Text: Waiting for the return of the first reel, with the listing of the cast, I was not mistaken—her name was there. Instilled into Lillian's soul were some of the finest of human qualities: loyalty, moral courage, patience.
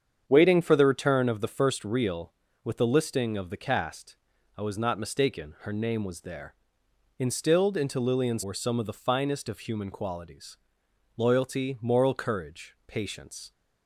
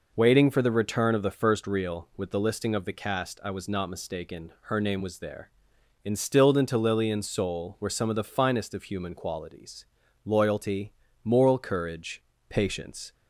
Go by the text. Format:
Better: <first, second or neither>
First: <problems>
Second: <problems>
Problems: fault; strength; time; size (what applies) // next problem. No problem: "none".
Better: second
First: starts louder than the rest; strong; until 1.2 s; 8 dB // skips "soul"; at 8.4 s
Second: none